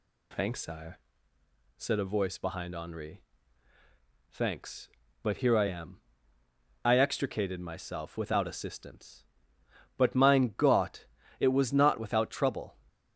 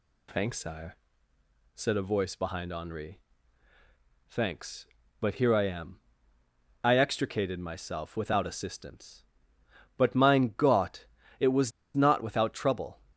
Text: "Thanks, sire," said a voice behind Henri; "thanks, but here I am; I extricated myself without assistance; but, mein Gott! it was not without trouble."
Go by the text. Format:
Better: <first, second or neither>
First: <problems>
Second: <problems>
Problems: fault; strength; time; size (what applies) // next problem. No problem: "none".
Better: first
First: none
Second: pauses between "was" and "not"; slight; at 11.7 s; 0.25 s long